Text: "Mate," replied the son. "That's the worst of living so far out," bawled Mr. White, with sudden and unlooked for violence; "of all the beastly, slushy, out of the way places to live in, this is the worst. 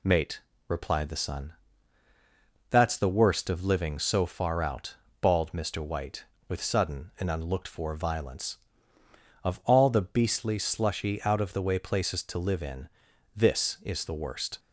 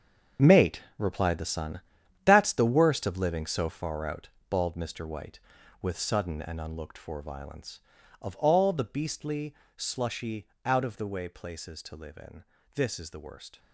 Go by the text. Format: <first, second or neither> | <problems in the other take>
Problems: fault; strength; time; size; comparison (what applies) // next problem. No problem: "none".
first | gets quieter; strong; throughout; 12 dB